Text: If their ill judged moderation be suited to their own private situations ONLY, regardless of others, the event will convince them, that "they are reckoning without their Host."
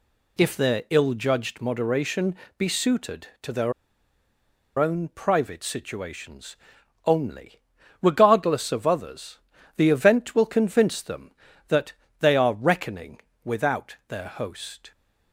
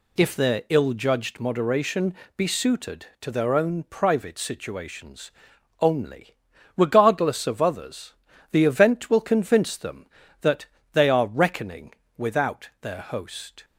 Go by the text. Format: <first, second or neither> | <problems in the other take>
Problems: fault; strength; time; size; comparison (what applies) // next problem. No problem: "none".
second | pauses between "moderation" and "be"; slight; at 2.3 s; 0.24 s long; slight in the second // pauses between "their" and "own"; at 3.7 s; 1.0 s long // pauses between "situations" and "ONLY"; noticeable; at 6.5 s; 0.50 s long; noticeable in the second // pauses between "that" and "they"; slight; at 11.9 s; 0.26 s long; slight in the second // pauses between "reckoning" and "without"; slight; at 13.1 s; 0.24 s long; slight in the second